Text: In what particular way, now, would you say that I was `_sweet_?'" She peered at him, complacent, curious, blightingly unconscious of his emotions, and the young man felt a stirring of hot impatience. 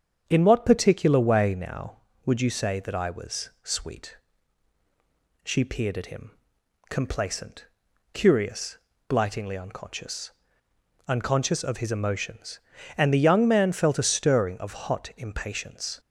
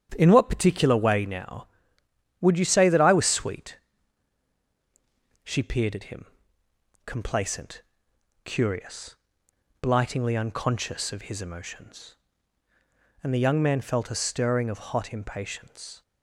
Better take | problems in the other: second | starts louder than the rest; strong; until 1.2 s; 8 dB; strong in the second // says "unconscious" twice; at 11.0 s

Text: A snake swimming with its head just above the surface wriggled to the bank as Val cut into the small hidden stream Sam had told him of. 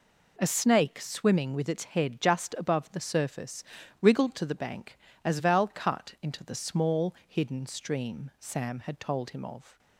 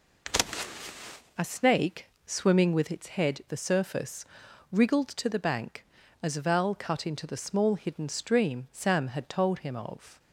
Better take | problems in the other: first | pauses between "snake" and "swimming"; slight; at 2.0 s; 0.18 s long // skips "just above"; at 3.4 s // pauses between "surface" and "wriggled"; noticeable; at 4.2 s; 0.46 s long; also in the first

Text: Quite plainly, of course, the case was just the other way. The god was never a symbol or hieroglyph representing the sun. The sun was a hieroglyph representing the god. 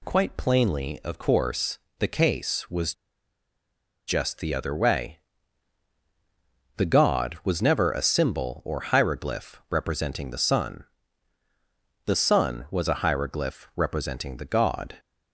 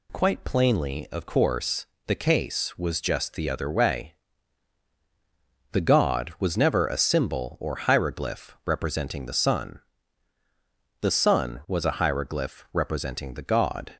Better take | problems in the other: second | pauses between "was" and "just"; at 2.9 s; 1.1 s long

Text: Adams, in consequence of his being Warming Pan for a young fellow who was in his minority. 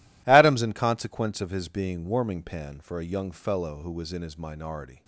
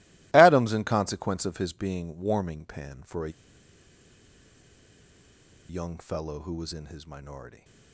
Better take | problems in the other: first | pauses between "a" and "young"; strong; at 3.2 s; 2.3 s long

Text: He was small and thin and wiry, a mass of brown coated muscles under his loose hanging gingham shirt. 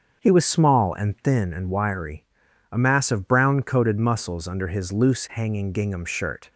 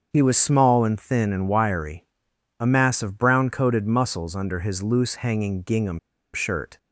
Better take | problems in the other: first | starts louder than the rest; until 1.1 s; 7 dB; also in the first // pauses between "gingham" and "shirt"; slight; at 5.9 s; 0.36 s long

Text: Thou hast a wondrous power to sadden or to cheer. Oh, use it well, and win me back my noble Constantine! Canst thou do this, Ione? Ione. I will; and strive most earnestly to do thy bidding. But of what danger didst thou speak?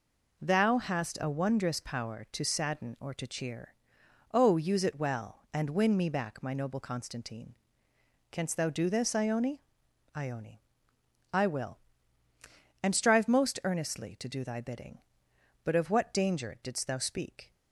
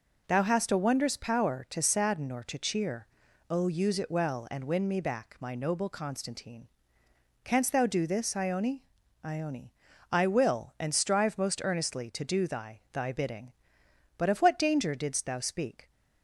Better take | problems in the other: first | says "thy" twice; at 12.9 s

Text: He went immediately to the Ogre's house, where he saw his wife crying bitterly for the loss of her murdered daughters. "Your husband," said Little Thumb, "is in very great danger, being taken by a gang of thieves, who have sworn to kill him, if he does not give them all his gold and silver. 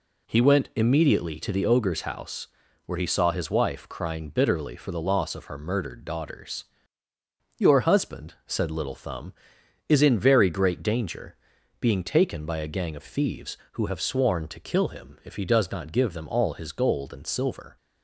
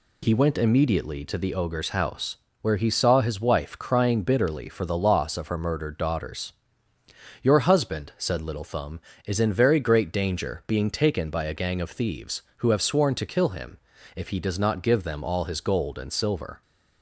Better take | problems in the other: neither | none

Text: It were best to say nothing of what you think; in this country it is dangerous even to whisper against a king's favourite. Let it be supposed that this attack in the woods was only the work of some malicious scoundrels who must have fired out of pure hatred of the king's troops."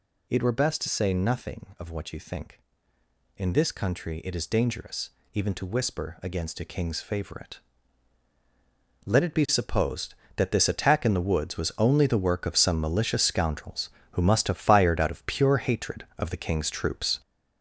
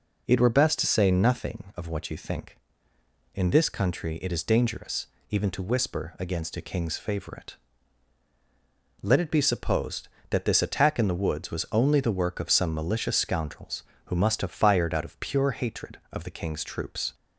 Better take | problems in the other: second | gets louder; noticeable; throughout; 5.5 dB // pauses between "dangerous" and "even"; slight; at 5.0 s; 0.24 s long; slight in the second

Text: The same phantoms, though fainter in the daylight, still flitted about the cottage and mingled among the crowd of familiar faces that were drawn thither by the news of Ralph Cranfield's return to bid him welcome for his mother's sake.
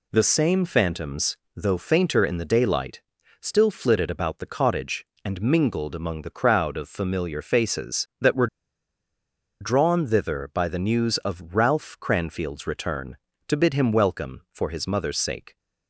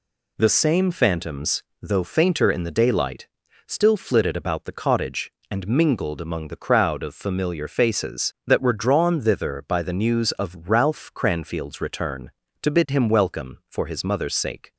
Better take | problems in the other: second | pauses between "were" and "drawn"; at 8.4 s; 1.1 s long

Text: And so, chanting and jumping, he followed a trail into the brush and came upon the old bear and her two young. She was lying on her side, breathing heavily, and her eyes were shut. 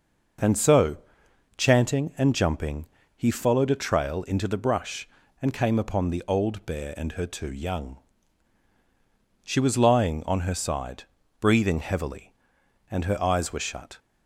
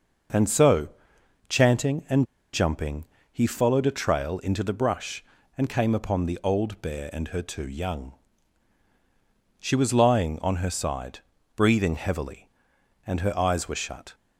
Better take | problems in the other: first | pauses between "and" and "jumping"; slight; at 2.2 s; 0.28 s long

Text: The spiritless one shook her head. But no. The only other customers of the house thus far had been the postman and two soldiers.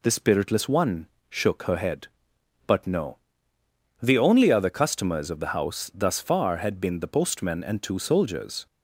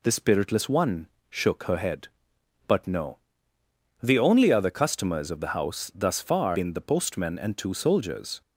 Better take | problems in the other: first | pauses between "one" and "shook"; slight; at 1.0 s; 0.22 s long; slight in the first // skips "had"; at 6.5 s

